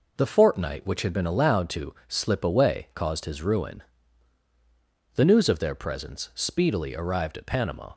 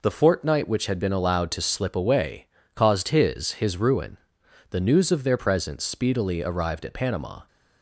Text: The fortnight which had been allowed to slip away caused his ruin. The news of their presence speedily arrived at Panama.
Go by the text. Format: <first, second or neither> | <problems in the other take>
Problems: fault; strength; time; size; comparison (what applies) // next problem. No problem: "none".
first | pauses between "away" and "caused"; slight; at 2.4 s; 0.30 s long // says "his" twice; at 3.5 s